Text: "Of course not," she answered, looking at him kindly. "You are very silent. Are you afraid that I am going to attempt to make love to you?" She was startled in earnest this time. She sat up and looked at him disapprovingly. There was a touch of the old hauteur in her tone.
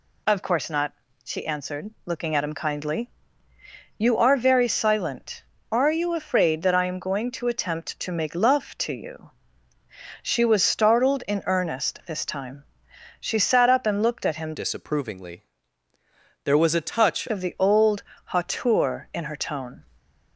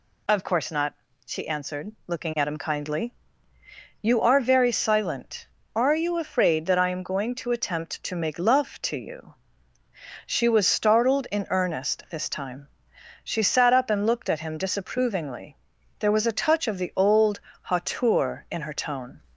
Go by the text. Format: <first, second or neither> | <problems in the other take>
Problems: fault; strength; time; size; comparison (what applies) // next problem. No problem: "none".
second | changes voice from "disapprovingly" to "touch"; from 14.5 to 17.2 s; 2.7 s long // pauses between "old" and "hauteur"; slight; at 18.0 s; 0.22 s long; slight in the second